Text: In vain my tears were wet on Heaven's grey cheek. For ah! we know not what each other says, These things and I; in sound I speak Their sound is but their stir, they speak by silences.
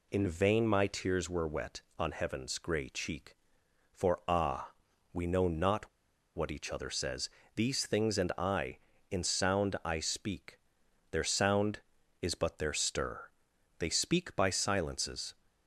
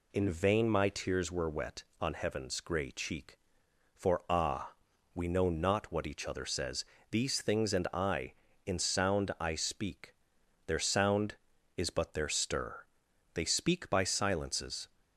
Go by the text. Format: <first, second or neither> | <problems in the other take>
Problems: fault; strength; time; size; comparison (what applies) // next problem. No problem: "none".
second | pauses between "not" and "what"; noticeable; at 5.8 s; 0.47 s long // pauses between "speak" and "Their"; noticeable; at 10.5 s; 0.52 s long; noticeable in the second